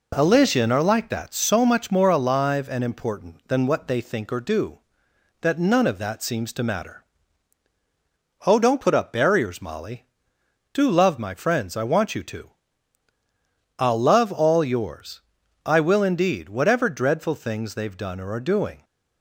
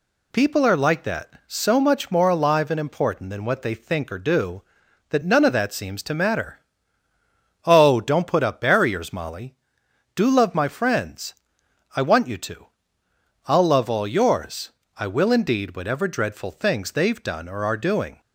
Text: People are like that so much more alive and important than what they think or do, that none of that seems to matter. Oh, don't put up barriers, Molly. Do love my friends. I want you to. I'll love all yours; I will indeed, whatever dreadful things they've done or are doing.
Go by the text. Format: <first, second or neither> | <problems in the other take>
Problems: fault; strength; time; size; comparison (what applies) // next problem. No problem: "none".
second | says "Elysian" for "People"; at 0.1 s